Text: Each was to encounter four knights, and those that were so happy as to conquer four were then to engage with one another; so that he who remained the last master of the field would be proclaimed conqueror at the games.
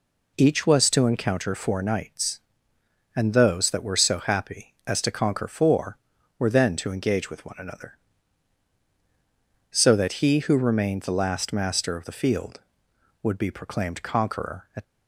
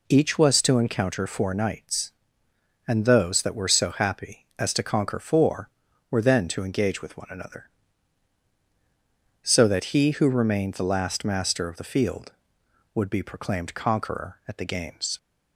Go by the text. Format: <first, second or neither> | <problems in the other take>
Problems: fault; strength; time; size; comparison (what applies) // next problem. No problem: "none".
second | stops before "the games"; at 14.8 s